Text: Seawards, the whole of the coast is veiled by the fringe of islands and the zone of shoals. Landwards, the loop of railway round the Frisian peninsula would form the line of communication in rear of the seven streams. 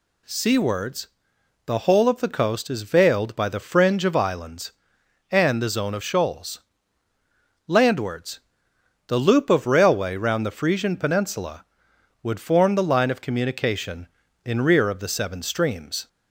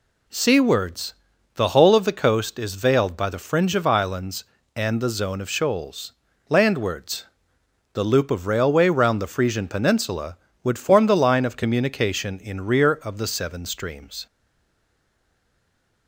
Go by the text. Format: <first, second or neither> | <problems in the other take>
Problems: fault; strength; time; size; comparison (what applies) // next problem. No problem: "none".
first | stays silent after the last word; noticeable; from 14.2 s on; 1.8 s long